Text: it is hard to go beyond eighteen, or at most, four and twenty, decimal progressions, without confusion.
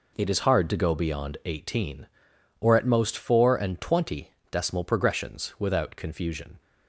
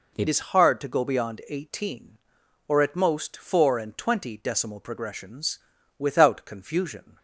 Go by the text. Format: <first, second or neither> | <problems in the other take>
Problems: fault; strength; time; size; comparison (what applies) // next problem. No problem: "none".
first | changes voice at "is"; from 0.2 s on; 6.9 s long